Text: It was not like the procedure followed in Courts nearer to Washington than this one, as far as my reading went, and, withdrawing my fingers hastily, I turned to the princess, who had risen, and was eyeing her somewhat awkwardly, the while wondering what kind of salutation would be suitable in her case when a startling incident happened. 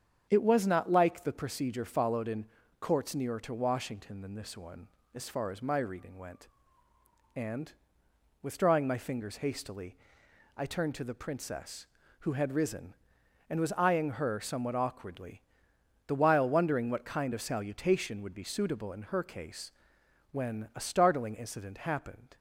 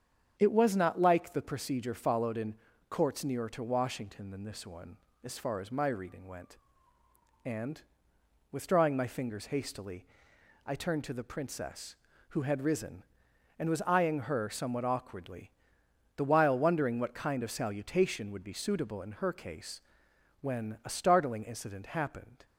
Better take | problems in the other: neither | starts louder than the rest; strong; the same in both // pauses between "in" and "Courts"; slight; the same in both // pauses between "case" and "when"; noticeable; the same in both

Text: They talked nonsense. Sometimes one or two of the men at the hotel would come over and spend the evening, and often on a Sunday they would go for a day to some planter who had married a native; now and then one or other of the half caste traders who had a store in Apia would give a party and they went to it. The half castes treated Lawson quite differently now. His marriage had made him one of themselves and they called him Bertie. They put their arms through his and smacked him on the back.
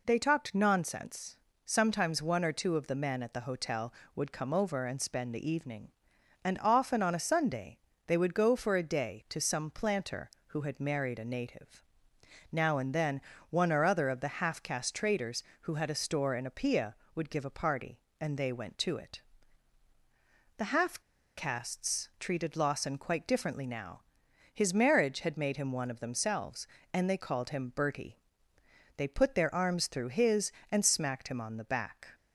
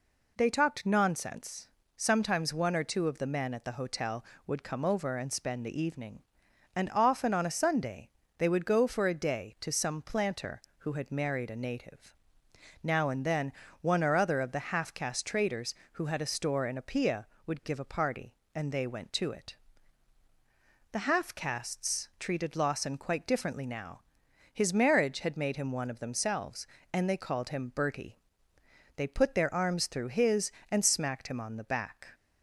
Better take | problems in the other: second | pauses between "Sunday" and "they"; slight; at 7.7 s; 0.30 s long; slight in the second // pauses between "then" and "one"; slight; at 13.2 s; 0.30 s long; slight in the second // pauses between "half" and "castes"; at 20.9 s; 0.37 s long

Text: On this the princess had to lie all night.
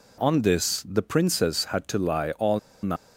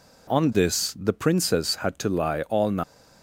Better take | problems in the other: second | pauses between "all" and "night"; slight; at 2.5 s; 0.23 s long

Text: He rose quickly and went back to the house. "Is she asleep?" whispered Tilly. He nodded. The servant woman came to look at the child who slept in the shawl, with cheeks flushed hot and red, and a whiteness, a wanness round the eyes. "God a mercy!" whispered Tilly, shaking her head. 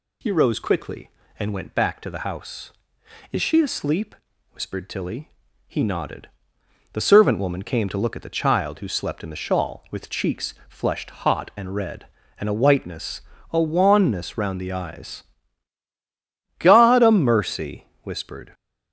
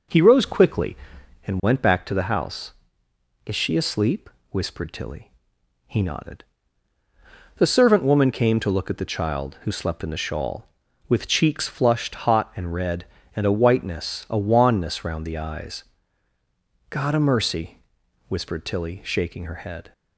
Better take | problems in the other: second | pauses between "cheeks" and "flushed"; slight; at 10.5 s; 0.16 s long // stops before "Tilly shaking her head"; at 18.5 s

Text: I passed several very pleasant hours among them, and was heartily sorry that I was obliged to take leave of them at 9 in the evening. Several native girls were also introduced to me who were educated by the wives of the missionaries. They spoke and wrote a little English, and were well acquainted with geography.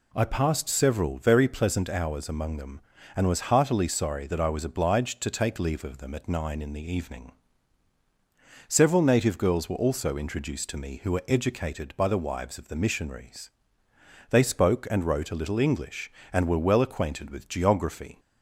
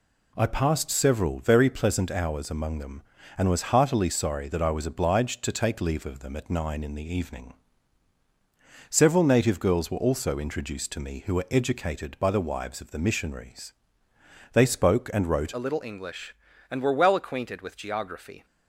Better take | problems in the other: first | changes voice at "a"; from 15.5 s on; 2.9 s long

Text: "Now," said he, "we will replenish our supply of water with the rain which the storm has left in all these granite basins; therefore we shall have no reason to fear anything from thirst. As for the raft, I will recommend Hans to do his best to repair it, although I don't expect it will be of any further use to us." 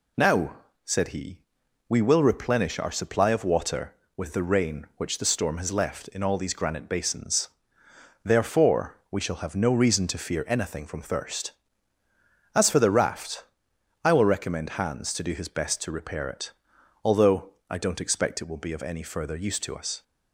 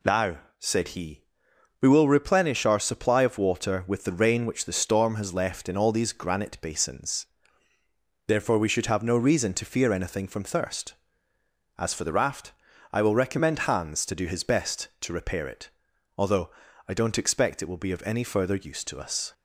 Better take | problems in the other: first | says "should" for "shall"; at 8.6 s // pauses between "although" and "I"; at 16.5 s; 0.38 s long; slight in the first

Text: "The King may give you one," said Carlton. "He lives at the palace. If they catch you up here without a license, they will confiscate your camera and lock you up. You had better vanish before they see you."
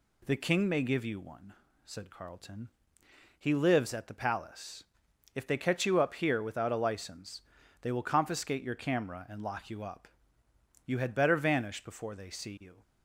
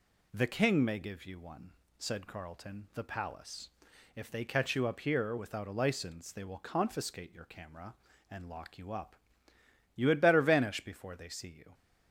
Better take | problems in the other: first | skips "He lives at"; at 2.9 s

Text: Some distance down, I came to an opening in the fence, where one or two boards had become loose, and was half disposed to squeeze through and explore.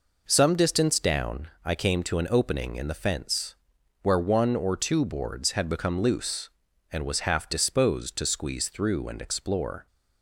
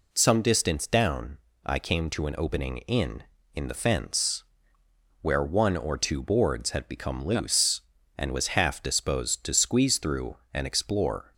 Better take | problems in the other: first | says "in" twice; at 3.5 s

